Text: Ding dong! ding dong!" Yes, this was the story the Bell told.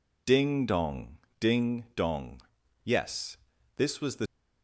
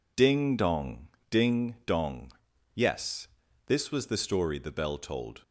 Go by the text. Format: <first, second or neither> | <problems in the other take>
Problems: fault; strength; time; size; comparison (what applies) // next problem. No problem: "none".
second | stops before "story the Bell told"; at 4.2 s